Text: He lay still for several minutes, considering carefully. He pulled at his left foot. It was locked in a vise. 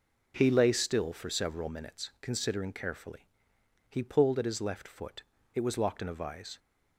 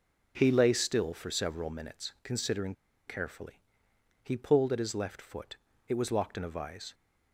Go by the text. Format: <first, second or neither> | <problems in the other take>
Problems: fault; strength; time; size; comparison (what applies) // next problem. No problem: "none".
first | pauses between "considering" and "carefully"; slight; at 2.7 s; 0.33 s long